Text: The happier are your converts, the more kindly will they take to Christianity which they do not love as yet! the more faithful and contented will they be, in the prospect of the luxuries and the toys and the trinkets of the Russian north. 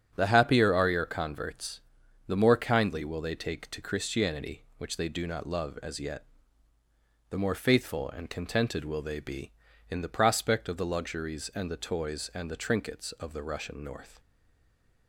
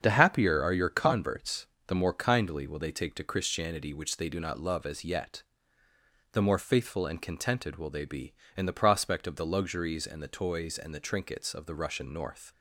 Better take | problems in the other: second | starts louder than the rest; strong; until 1.1 s; 7.5 dB; strong in the second // stays silent after the last word; slight; from 14.1 s on; 0.9 s long

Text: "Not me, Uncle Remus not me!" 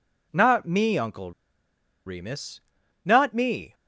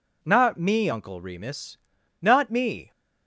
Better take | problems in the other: second | pauses between "Uncle" and "Remus"; noticeable; at 1.3 s; 0.75 s long // pauses between "Remus" and "not"; at 2.5 s; 0.44 s long; also in the second

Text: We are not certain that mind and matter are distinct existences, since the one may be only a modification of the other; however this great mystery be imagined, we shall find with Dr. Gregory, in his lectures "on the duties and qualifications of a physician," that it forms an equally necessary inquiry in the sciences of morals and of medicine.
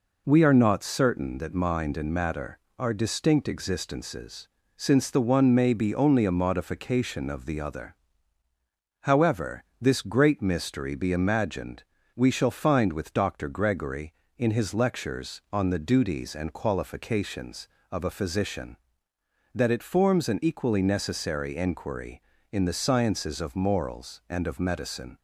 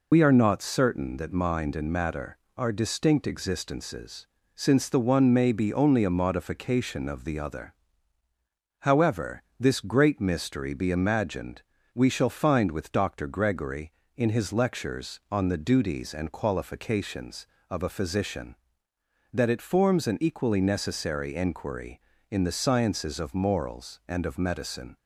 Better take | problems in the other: first | loses the start of "We"; at 0.1 s; 65 ms // pauses between "however" and "this"; slight; at 9.4 s; 0.18 s long; slight in the first

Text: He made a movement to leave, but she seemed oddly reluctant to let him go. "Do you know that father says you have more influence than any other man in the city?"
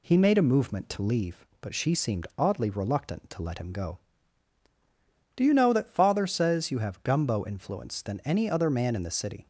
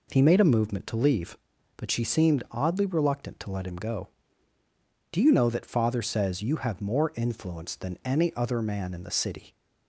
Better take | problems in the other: second | says "gumbo" for "more"; at 7.0 s

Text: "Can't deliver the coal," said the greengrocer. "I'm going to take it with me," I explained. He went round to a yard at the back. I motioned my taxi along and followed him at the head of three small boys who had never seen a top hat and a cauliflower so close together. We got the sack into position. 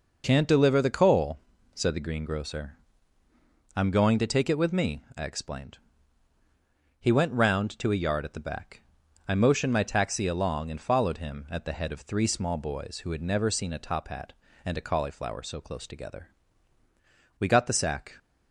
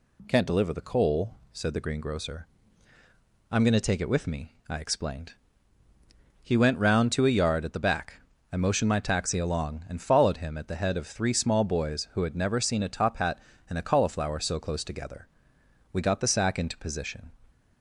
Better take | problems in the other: second | stops before "into position"; at 18.1 s

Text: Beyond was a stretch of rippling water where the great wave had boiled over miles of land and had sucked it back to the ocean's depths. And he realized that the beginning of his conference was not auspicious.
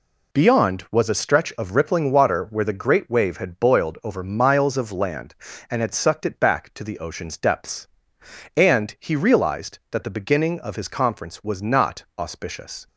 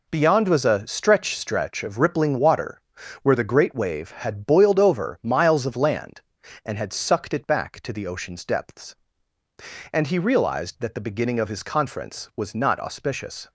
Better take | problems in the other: first | says "stretch" twice; at 1.3 s // pauses between "water" and "where"; at 2.7 s; 0.44 s long

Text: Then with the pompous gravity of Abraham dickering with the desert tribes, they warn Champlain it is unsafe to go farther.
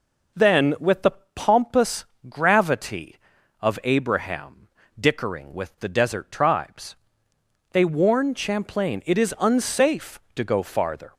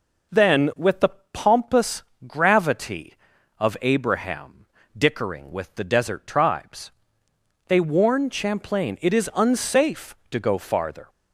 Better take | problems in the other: neither | pauses between "the" and "pompous"; slight; the same in both // pauses between "pompous" and "gravity"; slight; the same in both // pauses between "Abraham" and "dickering"; slight; the same in both

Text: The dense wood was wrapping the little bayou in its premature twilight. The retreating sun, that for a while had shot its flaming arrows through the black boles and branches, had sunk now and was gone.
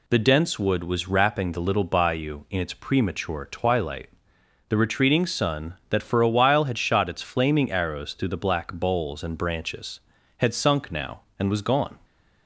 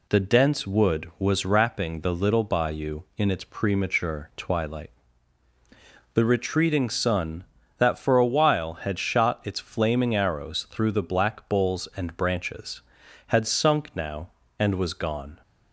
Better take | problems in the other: neither | none

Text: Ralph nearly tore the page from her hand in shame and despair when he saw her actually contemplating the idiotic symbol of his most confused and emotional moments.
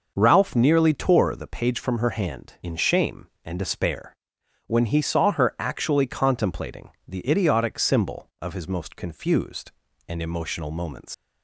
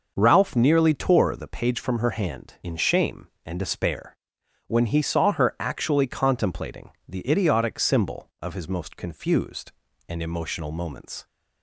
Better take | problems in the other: second | pauses between "despair" and "when"; noticeable; at 4.1 s; 0.54 s long; noticeable in the second // pauses between "contemplating" and "the"; slight; at 6.8 s; 0.18 s long; slight in the second // leaves "moments" unfinished; at 11.1 s; 110 ms

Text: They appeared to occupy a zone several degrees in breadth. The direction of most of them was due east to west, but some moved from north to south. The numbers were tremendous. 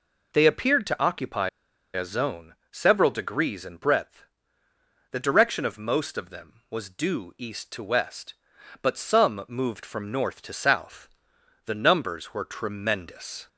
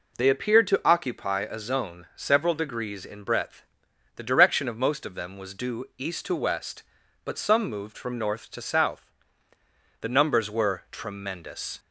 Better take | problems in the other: second | pauses between "occupy" and "a"; at 1.4 s; 0.44 s long // pauses between "zone" and "several"; slight; at 2.5 s; 0.18 s long

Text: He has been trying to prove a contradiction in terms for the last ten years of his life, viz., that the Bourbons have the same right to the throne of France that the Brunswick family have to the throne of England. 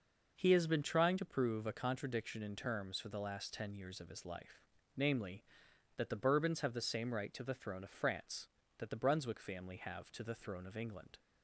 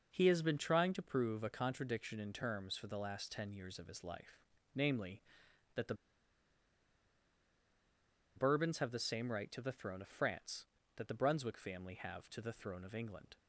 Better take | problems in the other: first | pauses between "the" and "Bourbons"; strong; at 5.9 s; 2.4 s long

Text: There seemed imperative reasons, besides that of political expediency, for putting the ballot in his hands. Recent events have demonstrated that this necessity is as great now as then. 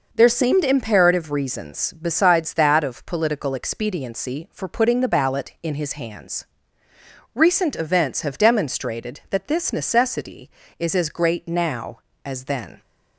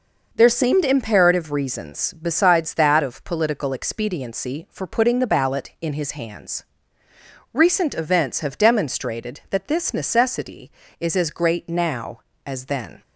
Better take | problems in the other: neither | none

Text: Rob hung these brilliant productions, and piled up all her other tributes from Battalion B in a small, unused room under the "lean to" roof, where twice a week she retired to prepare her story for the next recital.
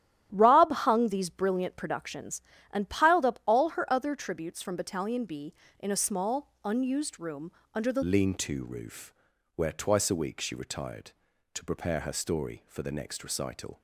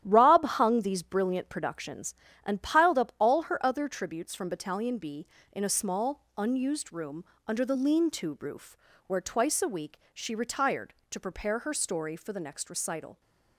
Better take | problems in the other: second | starts louder than the rest; strong; until 1.3 s; 11.5 dB; strong in the second // pauses between "room" and "under"; slight; at 7.5 s; 0.22 s long; slight in the second // changes voice at "lean"; from 8.0 s on; 5.8 s long

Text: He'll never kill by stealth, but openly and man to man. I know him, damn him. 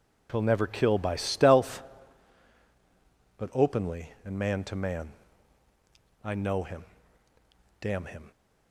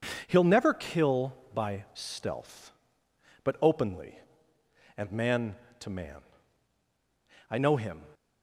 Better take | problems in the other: first | stops before "damn him"; at 8.1 s

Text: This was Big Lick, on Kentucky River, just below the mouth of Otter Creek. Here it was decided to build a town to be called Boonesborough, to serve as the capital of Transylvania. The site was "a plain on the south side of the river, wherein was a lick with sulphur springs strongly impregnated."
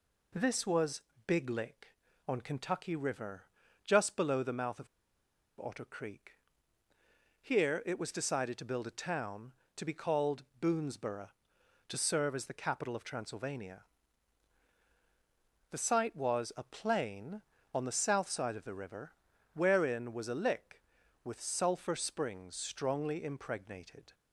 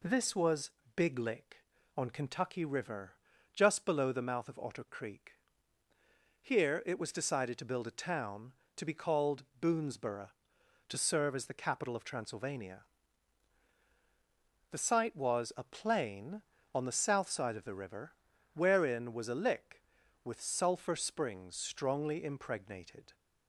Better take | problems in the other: second | pauses between "was" and "Big"; slight; at 1.0 s; 0.26 s long; slight in the second // pauses between "of" and "Otter"; noticeable; at 4.8 s; 0.74 s long // pauses between "called" and "Boonesborough"; slight; at 10.4 s; 0.18 s long; slight in the second

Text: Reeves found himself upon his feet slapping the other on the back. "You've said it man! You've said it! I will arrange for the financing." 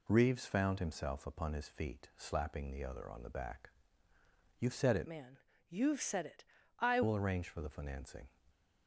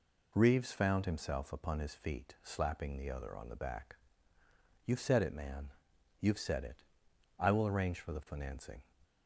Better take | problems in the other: second | changes voice from "man" to "I"; from 5.0 to 7.0 s; 2.0 s long

